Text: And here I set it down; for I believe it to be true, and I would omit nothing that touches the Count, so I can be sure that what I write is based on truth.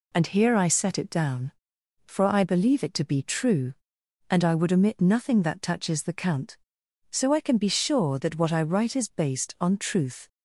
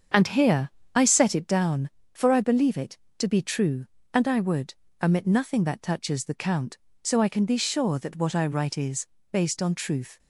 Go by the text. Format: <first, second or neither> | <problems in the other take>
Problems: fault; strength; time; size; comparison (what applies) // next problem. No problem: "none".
first | starts louder than the rest; strong; until 1.6 s; 7 dB // pauses between "here" and "I"; slight; at 0.6 s; 0.26 s long // pauses between "would" and "omit"; slight; at 4.7 s; 0.28 s long // pauses between "is" and "based"; slight; at 9.0 s; 0.26 s long